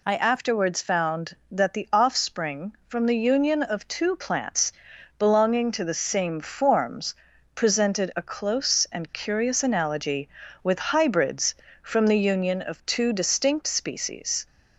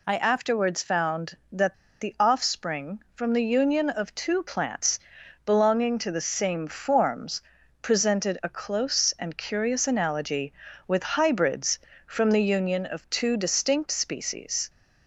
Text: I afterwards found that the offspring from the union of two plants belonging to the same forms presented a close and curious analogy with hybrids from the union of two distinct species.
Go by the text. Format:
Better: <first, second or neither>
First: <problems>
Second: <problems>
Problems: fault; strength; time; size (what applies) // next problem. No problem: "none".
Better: first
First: pauses between "plants" and "belonging"; at 4.7 s; 0.44 s long // pauses between "forms" and "presented"; at 7.1 s; 0.40 s long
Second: pauses between "that" and "the"; slight; at 1.7 s; 0.26 s long // pauses between "plants" and "belonging"; at 4.9 s; 0.44 s long // pauses between "forms" and "presented"; at 7.4 s; 0.40 s long